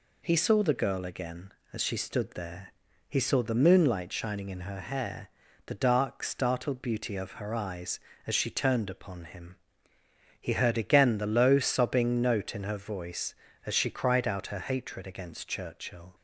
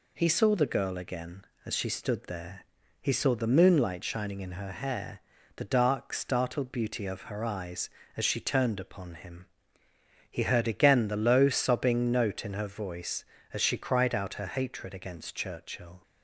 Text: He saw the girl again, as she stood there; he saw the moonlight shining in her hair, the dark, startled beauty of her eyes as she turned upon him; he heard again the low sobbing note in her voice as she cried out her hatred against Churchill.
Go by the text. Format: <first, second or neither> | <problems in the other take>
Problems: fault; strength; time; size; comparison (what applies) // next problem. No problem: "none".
neither | none